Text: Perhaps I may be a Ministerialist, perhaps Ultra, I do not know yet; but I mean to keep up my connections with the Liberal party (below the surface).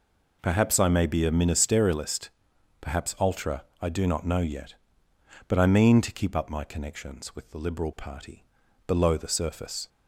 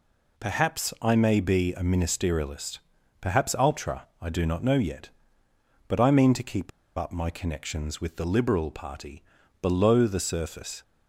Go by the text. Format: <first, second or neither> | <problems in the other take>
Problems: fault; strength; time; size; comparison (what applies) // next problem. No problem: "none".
first | pauses between "keep" and "up"; slight; at 6.7 s; 0.27 s long